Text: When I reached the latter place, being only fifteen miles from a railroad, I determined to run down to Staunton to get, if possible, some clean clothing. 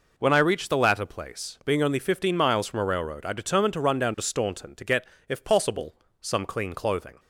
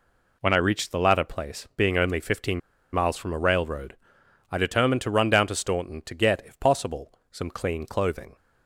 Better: first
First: none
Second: pauses between "fifteen" and "miles"; slight; at 2.6 s; 0.33 s long

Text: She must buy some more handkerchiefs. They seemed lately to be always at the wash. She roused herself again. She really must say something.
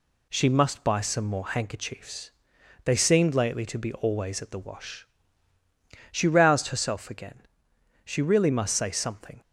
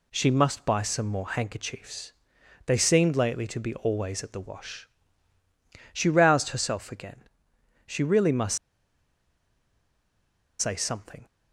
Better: first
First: none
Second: pauses between "must" and "say"; strong; at 8.5 s; 2.0 s long

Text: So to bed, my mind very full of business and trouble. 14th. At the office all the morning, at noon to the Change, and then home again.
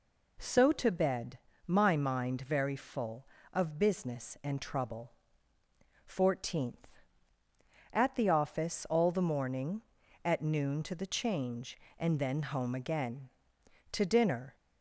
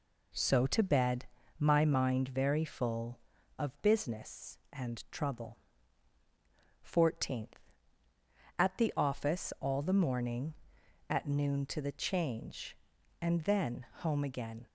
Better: second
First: goes on to say "To dinner"; noticeable; from 13.9 s on; 0.64 s long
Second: none

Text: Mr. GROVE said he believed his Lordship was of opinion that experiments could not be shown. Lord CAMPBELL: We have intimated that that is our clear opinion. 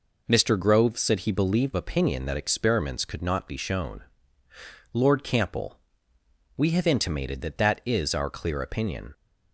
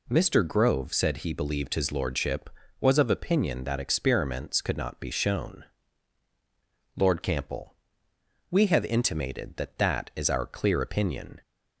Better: second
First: skips "his Lordship was of"; at 1.7 s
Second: none

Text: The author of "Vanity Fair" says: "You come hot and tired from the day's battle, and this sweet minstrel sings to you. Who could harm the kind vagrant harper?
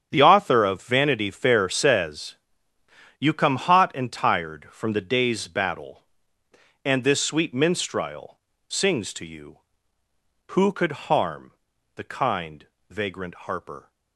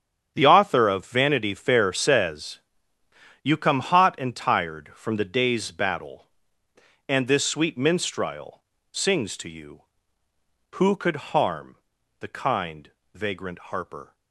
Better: neither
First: starts louder than the rest; strong; until 1.1 s; 8.5 dB // pauses between "minstrel" and "sings"; slight; at 8.3 s; 0.28 s long // pauses between "harm" and "the"; at 11.5 s; 0.44 s long // pauses between "kind" and "vagrant"; slight; at 12.6 s; 0.24 s long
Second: starts louder than the rest; strong; until 1.3 s; 8.5 dB // pauses between "minstrel" and "sings"; slight; at 8.6 s; 0.28 s long // pauses between "harm" and "the"; at 11.7 s; 0.44 s long // pauses between "kind" and "vagrant"; slight; at 12.8 s; 0.24 s long

